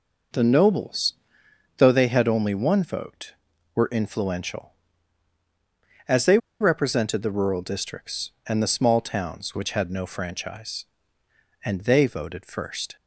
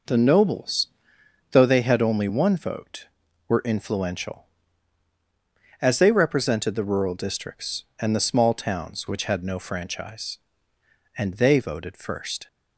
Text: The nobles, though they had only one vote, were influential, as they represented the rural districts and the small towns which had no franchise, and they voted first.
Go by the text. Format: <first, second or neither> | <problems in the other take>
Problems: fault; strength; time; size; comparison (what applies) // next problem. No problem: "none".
second | pauses between "they" and "represented"; slight; at 6.3 s; 0.23 s long